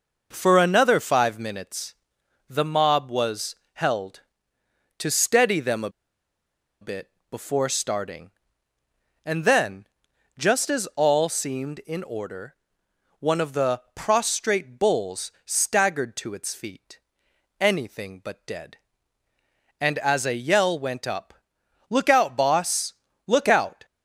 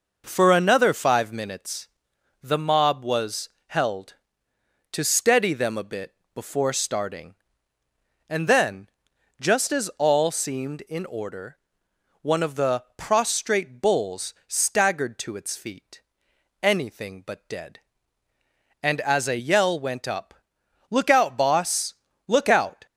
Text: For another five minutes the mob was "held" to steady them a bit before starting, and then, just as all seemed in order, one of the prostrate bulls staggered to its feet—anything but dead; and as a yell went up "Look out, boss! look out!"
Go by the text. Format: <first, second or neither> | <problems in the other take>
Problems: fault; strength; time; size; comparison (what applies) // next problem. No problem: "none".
second | pauses between "minutes" and "the"; noticeable; at 1.9 s; 0.56 s long; noticeable in the second // pauses between "was" and "held"; slight; at 3.5 s; 0.20 s long; slight in the second // pauses between "a" and "bit"; noticeable; at 5.8 s; 0.91 s long // pauses between "bit" and "before"; slight; at 7.1 s; 0.18 s long; slight in the second // pauses between "up" and "Look"; noticeable; at 21.3 s; 0.56 s long; noticeable in the second